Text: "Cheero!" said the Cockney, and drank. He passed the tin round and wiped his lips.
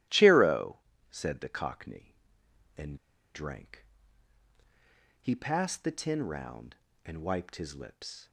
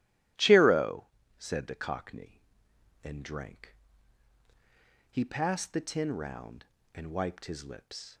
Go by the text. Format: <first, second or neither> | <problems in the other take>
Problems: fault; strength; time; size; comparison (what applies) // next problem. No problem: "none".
second | starts louder than the rest; strong; until 1.4 s; 14.5 dB; strong in the second // pauses between "and" and "drank"; at 2.9 s; 0.36 s long